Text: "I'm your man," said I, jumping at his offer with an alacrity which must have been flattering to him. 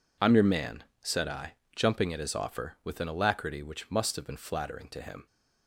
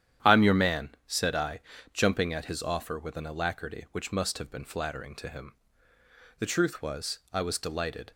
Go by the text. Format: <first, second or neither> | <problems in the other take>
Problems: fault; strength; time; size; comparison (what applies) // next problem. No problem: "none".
first | starts louder than the rest; strong; until 1.3 s; 10 dB // goes on to say "The truth was I was delighted"; strong; from 6.3 s on; 1.7 s long